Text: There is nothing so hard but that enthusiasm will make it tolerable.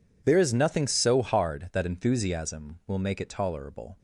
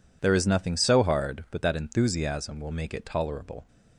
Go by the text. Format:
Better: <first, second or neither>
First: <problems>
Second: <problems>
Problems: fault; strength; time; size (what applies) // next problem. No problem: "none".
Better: second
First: skips "but"; at 1.6 s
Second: none